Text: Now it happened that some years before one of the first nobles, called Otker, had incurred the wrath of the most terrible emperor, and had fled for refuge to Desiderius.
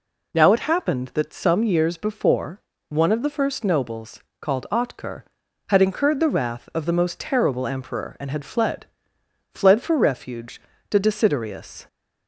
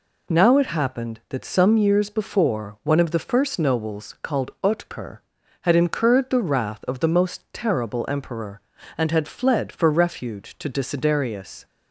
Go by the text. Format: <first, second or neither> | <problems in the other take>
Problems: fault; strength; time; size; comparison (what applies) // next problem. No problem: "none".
second | pauses between "before" and "one"; slight; at 2.6 s; 0.26 s long // says "fled" twice; at 9.5 s